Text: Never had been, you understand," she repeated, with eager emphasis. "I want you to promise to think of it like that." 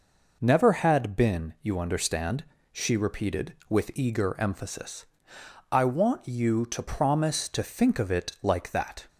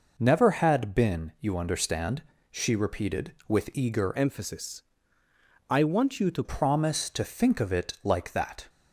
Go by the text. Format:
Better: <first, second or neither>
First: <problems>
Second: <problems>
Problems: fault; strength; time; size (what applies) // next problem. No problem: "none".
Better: first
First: none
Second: changes voice from "emphasis" to "to"; from 4.1 to 6.4 s; 2.3 s long